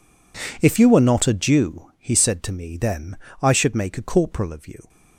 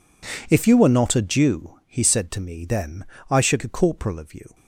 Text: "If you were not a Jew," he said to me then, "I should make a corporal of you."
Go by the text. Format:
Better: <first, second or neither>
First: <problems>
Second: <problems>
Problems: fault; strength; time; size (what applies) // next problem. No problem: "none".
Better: first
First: none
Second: skips "make"; at 3.6 s